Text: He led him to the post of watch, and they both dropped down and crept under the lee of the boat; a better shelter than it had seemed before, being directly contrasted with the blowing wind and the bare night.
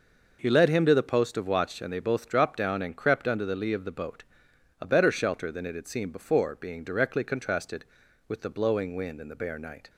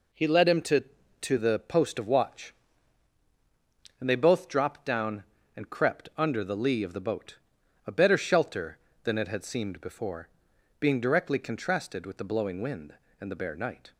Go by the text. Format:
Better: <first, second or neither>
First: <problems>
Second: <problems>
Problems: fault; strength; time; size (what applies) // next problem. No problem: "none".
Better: first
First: none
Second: says "to" twice; at 1.2 s